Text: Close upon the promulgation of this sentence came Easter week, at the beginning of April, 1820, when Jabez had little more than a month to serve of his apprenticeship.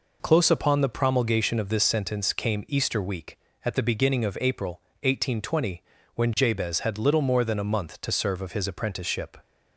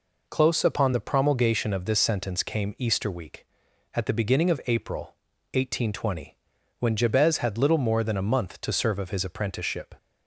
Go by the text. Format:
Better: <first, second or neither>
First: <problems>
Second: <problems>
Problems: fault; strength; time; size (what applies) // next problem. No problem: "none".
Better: neither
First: none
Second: none